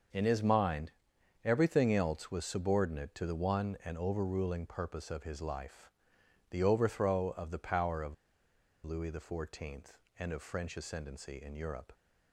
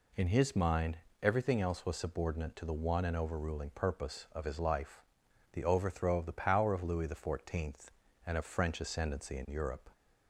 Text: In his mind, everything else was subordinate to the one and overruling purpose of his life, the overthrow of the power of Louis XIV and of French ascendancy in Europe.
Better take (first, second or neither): second